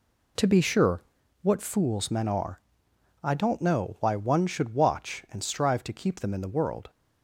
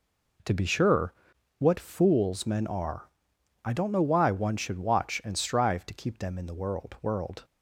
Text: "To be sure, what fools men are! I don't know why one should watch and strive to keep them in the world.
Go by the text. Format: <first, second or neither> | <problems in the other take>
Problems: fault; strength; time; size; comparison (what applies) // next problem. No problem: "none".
first | says "world" twice; at 7.0 s